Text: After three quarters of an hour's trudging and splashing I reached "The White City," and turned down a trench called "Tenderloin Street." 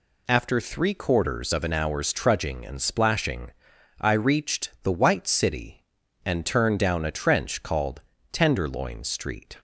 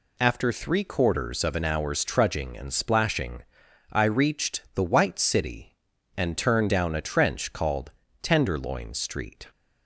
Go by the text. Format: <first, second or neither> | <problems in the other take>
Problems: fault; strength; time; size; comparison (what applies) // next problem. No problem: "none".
neither | pauses between "splashing" and "I"; noticeable; the same in both // pauses between "called" and "Tenderloin"; slight; the same in both